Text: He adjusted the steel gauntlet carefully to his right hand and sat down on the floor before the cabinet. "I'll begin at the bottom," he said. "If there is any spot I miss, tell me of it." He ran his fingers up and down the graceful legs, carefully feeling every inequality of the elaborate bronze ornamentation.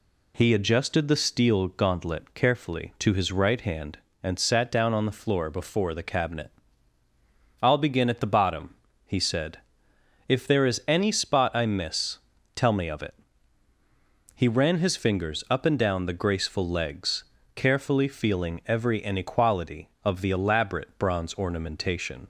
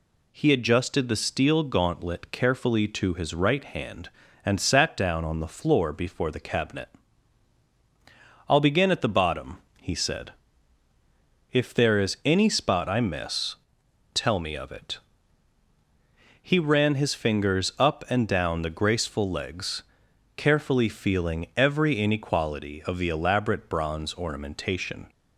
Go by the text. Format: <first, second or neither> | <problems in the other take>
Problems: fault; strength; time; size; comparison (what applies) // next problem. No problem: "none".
neither | none